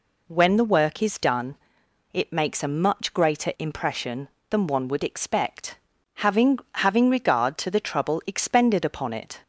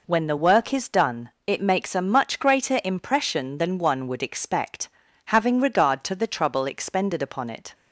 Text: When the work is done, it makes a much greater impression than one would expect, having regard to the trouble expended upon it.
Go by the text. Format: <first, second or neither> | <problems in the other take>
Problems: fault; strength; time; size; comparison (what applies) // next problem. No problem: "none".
second | says "having" twice; at 6.7 s